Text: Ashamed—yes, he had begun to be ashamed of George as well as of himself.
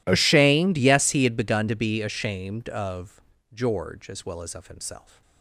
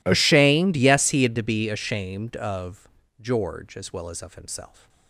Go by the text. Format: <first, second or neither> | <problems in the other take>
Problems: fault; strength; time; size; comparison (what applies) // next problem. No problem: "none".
first | skips "begun"; at 1.3 s // pauses between "of" and "George"; slight; at 2.8 s; 0.32 s long; slight in the first